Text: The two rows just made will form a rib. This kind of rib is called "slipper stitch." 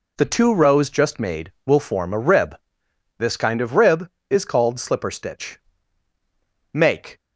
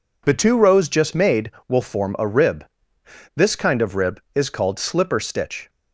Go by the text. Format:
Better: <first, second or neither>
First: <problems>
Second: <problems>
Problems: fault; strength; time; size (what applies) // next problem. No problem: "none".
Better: second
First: goes on to say "Make"; slight; from 6.7 s on; 0.48 s long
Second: none